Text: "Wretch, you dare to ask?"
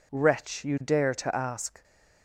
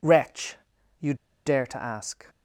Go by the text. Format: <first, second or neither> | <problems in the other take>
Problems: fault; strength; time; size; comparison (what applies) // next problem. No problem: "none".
first | pauses between "you" and "dare"; slight; at 1.1 s; 0.31 s long